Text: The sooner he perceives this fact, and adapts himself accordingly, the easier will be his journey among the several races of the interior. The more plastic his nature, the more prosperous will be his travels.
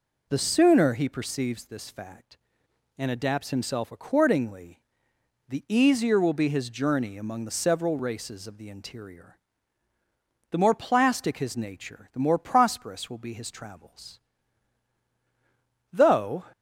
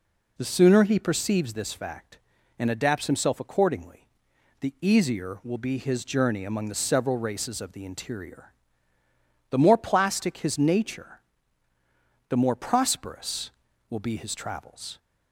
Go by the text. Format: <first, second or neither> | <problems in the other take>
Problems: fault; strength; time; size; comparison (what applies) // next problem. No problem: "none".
second | goes on to say "Though"; from 15.9 s on; 0.52 s long